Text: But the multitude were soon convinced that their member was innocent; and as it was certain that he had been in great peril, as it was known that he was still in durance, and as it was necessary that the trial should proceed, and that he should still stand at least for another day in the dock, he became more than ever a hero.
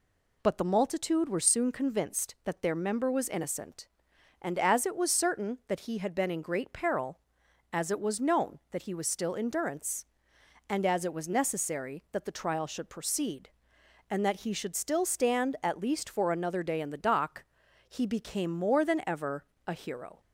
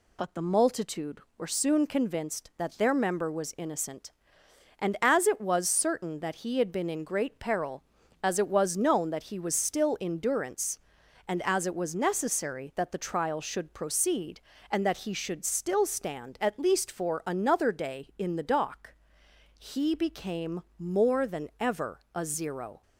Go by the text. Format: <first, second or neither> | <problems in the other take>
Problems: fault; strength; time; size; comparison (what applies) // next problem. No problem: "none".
first | pauses between "became" and "more"; slight; at 20.5 s; 0.18 s long // pauses between "ever" and "a"; slight; at 21.9 s; 0.16 s long; slight in the first // says "zero" for "hero"; at 22.2 s